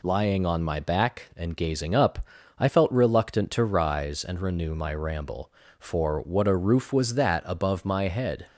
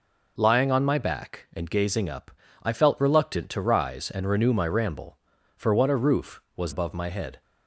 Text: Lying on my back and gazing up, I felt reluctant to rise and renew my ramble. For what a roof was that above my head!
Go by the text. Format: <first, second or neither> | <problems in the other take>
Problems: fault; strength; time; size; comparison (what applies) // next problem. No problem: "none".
first | skips "that"; at 6.7 s